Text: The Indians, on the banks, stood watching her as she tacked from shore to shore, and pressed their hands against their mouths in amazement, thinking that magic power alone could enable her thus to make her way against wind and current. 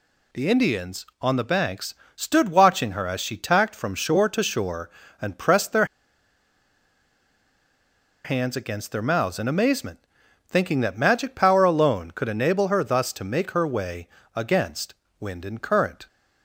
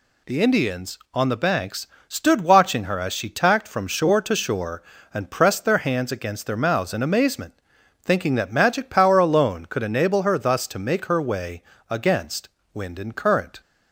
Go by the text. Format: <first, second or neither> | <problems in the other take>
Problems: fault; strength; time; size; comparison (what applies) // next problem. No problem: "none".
second | pauses between "their" and "hands"; strong; at 5.8 s; 2.3 s long // pauses between "way" and "against"; slight; at 14.0 s; 0.26 s long; slight in the second // pauses between "against" and "wind"; slight; at 14.9 s; 0.26 s long; slight in the second